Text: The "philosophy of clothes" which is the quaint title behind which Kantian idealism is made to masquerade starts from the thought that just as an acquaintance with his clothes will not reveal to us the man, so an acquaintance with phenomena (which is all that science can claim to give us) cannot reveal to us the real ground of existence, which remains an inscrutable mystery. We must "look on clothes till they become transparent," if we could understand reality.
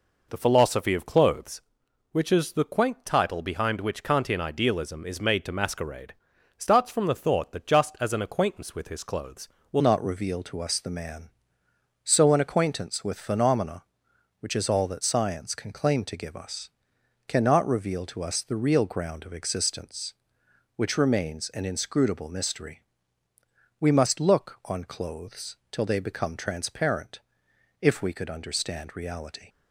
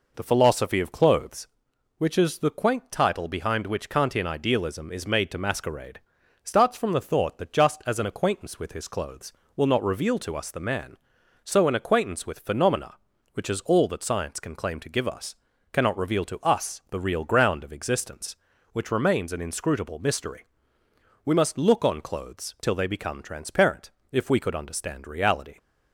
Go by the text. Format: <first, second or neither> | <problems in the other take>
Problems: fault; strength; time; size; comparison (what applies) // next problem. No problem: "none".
second | pauses between "masquerade" and "starts"; at 6.1 s; 0.42 s long; also in the second // changes voice at "not"; from 9.8 s on; 19.6 s long